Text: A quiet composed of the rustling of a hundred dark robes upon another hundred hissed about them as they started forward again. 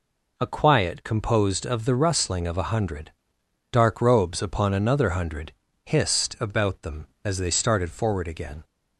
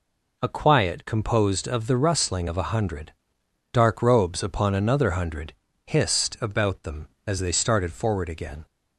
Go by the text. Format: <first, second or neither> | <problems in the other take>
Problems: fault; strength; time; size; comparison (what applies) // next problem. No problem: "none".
neither | pauses between "hundred" and "dark"; noticeable; the same in both // pauses between "hundred" and "hissed"; slight; the same in both